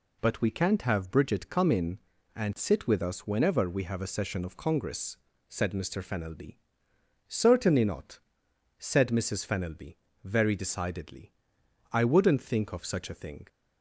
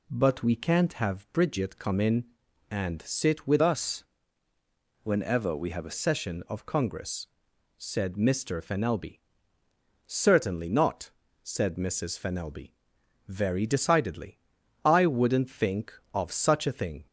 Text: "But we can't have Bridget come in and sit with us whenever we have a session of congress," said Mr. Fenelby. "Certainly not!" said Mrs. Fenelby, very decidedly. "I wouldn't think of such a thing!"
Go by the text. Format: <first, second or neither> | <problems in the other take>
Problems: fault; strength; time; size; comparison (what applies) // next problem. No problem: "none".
first | changes voice from "us" to "a"; from 3.6 to 5.9 s; 2.3 s long // pauses between "us" and "whenever"; noticeable; at 4.0 s; 0.98 s long